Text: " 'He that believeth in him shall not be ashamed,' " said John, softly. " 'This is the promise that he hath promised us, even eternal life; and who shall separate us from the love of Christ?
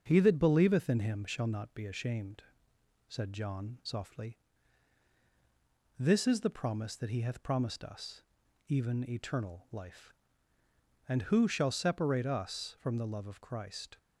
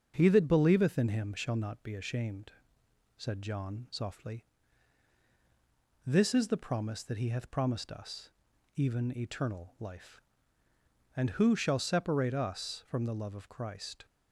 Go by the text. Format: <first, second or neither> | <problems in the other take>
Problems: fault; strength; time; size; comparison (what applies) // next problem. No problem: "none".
neither | starts louder than the rest; strong; the same in both